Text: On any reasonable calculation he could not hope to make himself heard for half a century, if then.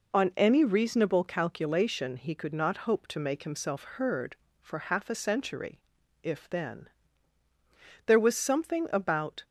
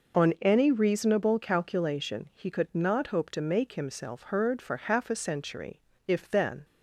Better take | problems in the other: second | goes on to say "There was something about"; from 8.0 s on; 1.3 s long

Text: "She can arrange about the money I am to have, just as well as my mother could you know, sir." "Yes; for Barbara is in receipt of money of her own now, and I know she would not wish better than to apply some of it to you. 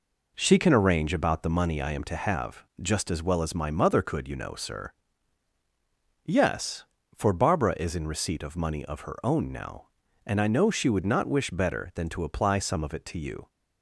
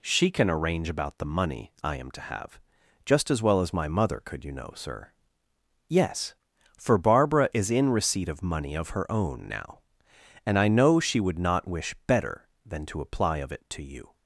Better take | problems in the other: first | skips "some"; at 13.3 s

